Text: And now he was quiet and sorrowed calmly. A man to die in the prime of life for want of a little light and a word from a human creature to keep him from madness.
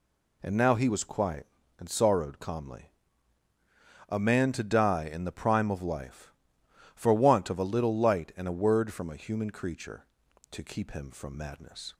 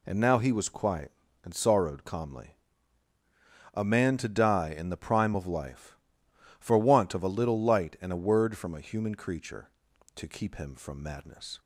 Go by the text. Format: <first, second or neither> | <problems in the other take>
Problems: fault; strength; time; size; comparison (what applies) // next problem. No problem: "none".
neither | none